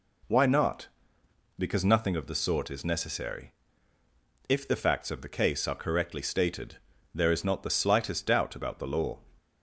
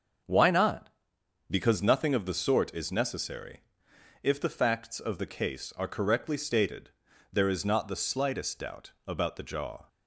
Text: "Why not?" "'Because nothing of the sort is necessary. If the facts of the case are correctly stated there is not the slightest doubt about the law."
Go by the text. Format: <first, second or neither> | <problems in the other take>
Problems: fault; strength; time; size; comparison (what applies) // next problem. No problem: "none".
first | starts louder than the rest; until 1.8 s; 6.5 dB // pauses between "stated" and "there"; at 6.9 s; 0.42 s long; also in the first // says "jaw" for "law"; at 9.4 s